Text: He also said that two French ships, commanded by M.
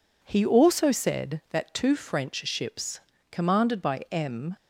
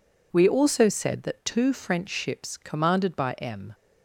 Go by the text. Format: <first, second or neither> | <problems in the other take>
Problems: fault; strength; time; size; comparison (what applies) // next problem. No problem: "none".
first | says "We" for "He"; at 0.3 s